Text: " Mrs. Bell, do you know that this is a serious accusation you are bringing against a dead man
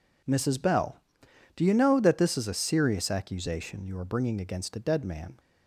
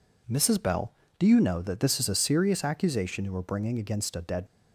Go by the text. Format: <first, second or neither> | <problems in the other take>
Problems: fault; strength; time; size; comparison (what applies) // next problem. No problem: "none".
first | stops before "man"; at 4.4 s